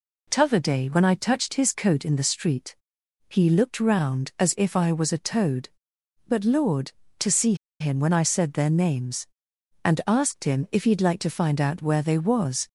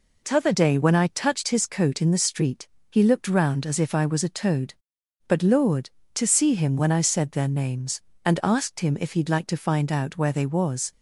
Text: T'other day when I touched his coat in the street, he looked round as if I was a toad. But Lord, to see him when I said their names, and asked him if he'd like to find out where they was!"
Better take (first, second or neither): second